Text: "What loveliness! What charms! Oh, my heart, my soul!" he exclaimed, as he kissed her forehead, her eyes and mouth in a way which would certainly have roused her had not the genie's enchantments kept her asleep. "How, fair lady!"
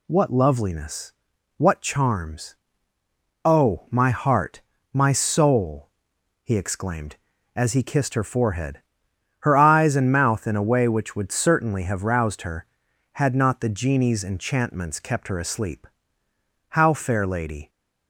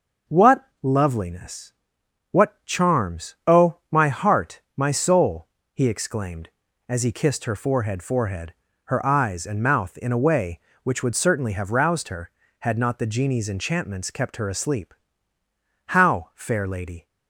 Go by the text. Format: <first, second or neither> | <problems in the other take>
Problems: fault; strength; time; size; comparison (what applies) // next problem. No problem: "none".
first | pauses between "What" and "loveliness"; slight; at 0.6 s; 0.16 s long // says "forehead" twice; at 8.0 s